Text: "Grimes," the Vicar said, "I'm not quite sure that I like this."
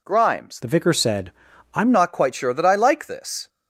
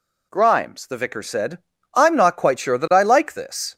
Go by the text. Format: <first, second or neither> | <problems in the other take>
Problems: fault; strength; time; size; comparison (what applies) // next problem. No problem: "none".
second | changes voice from "the" to "I'm"; from 0.6 to 1.9 s; 1.3 s long